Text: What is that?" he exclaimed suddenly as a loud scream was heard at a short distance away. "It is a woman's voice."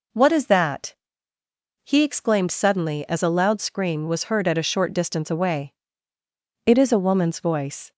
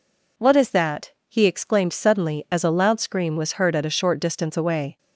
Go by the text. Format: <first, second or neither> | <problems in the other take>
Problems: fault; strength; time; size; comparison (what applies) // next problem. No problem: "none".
first | stops before "It is a woman's voice"; at 4.9 s